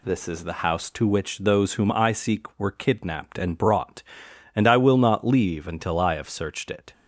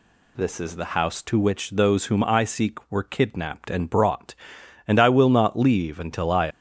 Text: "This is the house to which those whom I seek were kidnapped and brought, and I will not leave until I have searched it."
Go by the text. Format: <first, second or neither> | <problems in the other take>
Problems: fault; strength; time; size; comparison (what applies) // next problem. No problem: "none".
first | stops before "have searched it"; at 6.5 s